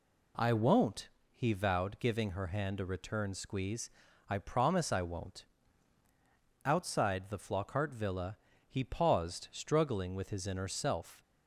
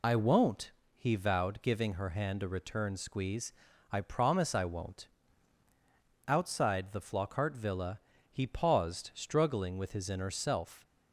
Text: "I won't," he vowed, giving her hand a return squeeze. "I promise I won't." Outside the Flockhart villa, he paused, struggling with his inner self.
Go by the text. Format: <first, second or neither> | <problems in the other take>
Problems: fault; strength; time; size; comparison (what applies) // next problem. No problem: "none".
first | loses the start of "I"; at 0.0 s; 65 ms